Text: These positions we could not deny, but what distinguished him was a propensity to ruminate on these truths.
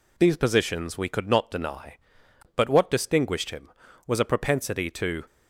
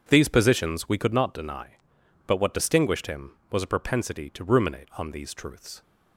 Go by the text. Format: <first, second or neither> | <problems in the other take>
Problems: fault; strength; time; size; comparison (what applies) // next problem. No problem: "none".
second | stops before "ruminate on these truths"; at 5.2 s